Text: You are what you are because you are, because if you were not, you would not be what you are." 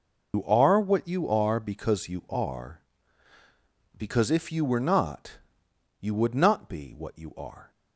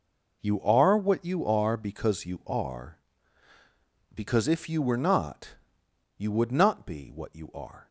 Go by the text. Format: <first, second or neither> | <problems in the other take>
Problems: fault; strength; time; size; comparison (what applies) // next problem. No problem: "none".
second | loses the start of "You"; at 0.3 s; 100 ms